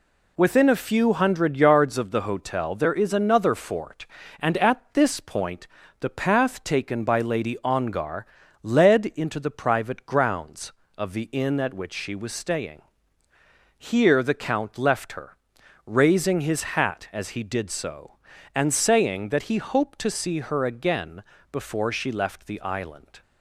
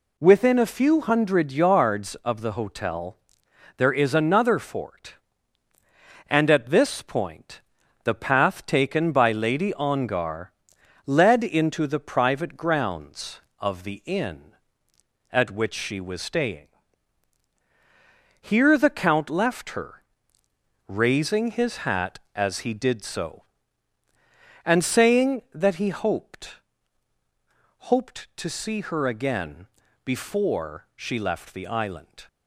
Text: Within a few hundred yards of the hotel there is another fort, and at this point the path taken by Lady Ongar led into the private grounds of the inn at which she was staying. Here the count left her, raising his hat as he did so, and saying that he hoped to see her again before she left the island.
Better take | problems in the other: first | pauses between "hotel" and "there"; noticeable; at 3.1 s; 0.60 s long // pauses between "point" and "the"; at 7.6 s; 0.42 s long; slight in the first // pauses between "Ongar" and "led"; noticeable; at 10.5 s; 0.54 s long; also in the first // says "hoped" twice; at 27.9 s // pauses between "again" and "before"; slight; at 29.6 s; 0.36 s long; slight in the first

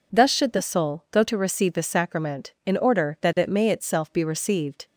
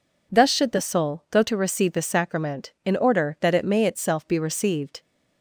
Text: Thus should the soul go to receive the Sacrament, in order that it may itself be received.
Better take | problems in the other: neither | none

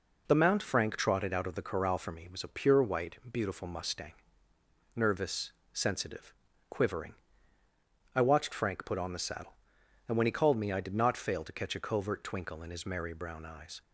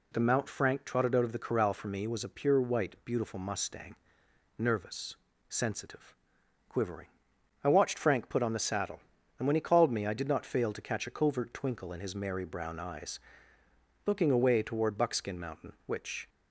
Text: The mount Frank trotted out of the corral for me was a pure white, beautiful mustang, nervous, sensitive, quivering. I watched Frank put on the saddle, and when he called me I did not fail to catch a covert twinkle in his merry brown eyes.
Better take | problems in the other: first | goes on to say "Looking away toward Buckskin Mountain which"; strong; from 14.0 s on; 2.2 s long

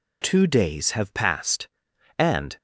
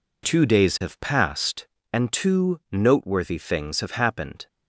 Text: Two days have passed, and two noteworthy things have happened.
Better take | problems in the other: second | stops before "two noteworthy things have happened"; at 2.5 s

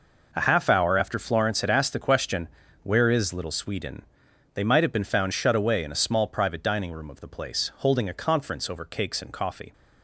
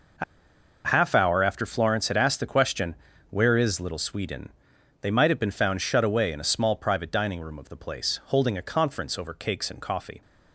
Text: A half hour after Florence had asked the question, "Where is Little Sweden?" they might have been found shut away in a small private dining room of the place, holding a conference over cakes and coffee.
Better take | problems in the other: first | pauses between "A" and "half"; noticeable; at 0.2 s; 0.62 s long

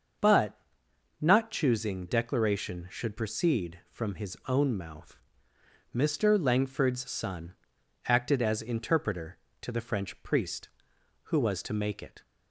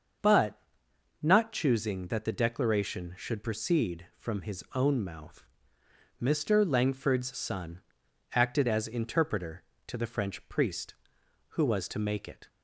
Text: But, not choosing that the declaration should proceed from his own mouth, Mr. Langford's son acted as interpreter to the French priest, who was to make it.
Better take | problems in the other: second | starts louder than the rest; until 1.8 s; 6.5 dB; also in the second // skips "that the"; at 2.0 s // pauses between "son" and "acted"; noticeable; at 7.5 s; 0.54 s long; noticeable in the second

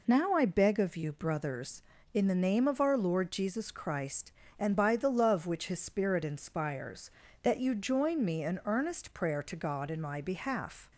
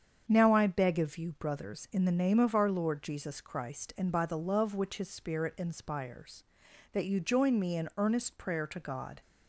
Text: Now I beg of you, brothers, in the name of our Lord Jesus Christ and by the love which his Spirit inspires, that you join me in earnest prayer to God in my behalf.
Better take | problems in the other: first | starts louder than the rest; strong; until 1.2 s; 7.5 dB // stops before "in my behalf"; at 9.2 s

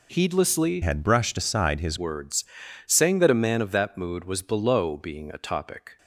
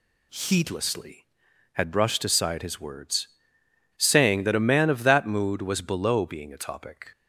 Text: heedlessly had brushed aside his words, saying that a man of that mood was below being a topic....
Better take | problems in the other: second | changes voice from "had" to "his"; from 0.8 to 1.9 s; 1.1 s long

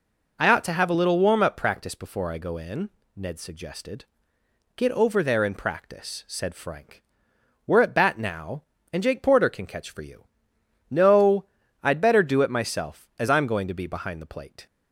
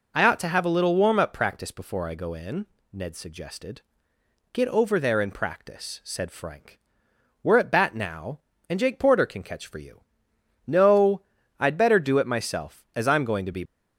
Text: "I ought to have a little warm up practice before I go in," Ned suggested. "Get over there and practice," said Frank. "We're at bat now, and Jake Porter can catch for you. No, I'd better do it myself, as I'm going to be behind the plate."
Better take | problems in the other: first | stops before "behind the plate"; at 13.6 s

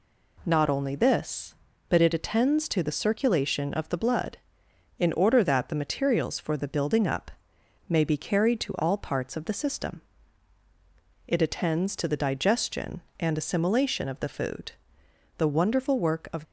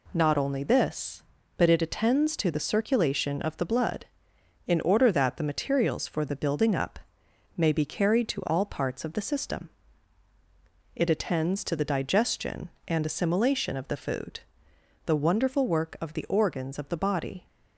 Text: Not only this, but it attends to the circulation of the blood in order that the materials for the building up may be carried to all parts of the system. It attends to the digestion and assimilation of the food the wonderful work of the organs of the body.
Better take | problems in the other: second | pauses between "up" and "may"; noticeable; at 7.3 s; 0.58 s long; noticeable in the second // pauses between "food" and "the"; noticeable; at 14.7 s; 0.64 s long; noticeable in the second // stops before "the organs of the body"; at 16.4 s

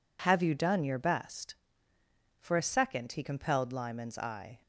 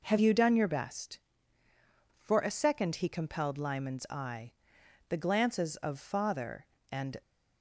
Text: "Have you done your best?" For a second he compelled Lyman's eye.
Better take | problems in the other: first | goes on to say "The glances of father and"; strong; from 5.0 s on; 2.1 s long

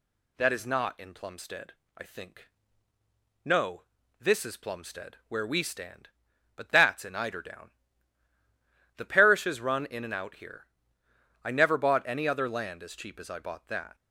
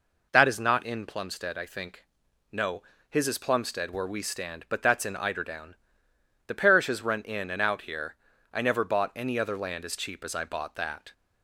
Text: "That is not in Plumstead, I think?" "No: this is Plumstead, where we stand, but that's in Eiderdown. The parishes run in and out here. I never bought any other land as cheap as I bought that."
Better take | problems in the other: first | says "his" for "this"; at 3.0 s

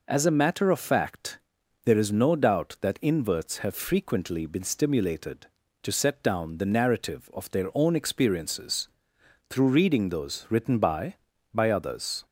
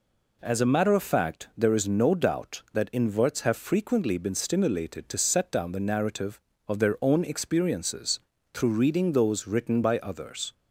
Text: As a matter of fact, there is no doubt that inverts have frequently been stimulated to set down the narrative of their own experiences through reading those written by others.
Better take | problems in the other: second | pauses between "experiences" and "through"; noticeable; at 8.8 s; 0.62 s long; slight in the second // says "by" twice; at 11.5 s

